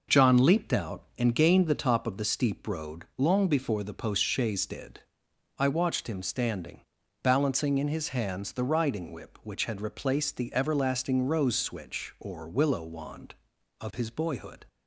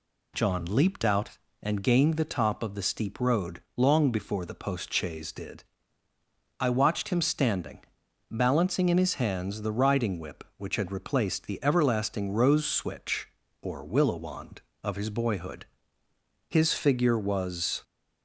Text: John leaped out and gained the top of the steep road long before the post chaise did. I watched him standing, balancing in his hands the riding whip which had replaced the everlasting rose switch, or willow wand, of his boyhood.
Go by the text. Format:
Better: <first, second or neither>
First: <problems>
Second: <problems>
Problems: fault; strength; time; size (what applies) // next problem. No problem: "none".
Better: first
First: none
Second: pauses between "road" and "long"; slight; at 3.6 s; 0.16 s long // goes on to say "His figure was"; from 16.4 s on; 1.3 s long